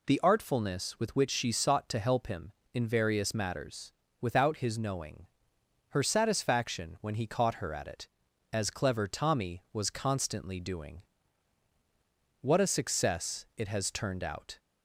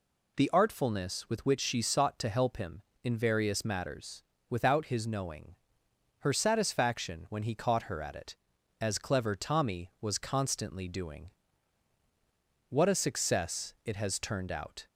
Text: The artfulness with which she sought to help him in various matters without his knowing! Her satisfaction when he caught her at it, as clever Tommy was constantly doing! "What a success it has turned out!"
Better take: neither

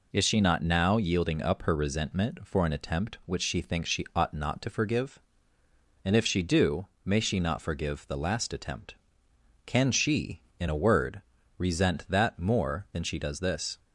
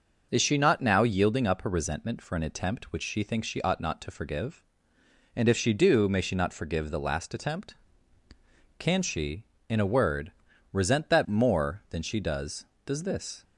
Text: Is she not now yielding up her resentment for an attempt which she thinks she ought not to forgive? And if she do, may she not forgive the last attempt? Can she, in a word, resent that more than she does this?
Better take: first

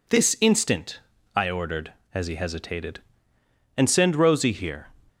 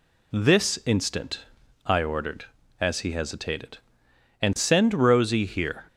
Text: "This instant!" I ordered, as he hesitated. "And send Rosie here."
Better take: neither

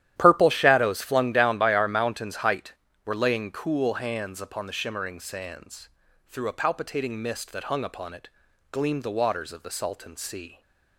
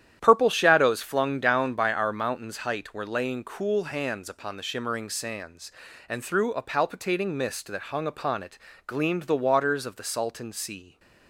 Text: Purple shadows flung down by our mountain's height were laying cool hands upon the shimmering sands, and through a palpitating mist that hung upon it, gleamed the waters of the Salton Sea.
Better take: second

